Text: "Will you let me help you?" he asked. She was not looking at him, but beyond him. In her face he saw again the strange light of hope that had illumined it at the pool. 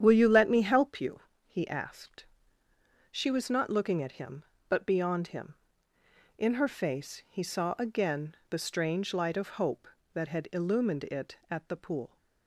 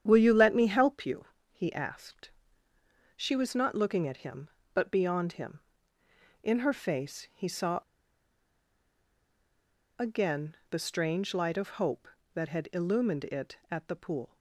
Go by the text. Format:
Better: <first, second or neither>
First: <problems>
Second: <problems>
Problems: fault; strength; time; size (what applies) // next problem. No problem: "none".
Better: first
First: starts louder than the rest; strong; until 1.0 s; 9 dB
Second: starts louder than the rest; strong; until 1.0 s; 9 dB // pauses between "saw" and "again"; strong; at 7.8 s; 2.1 s long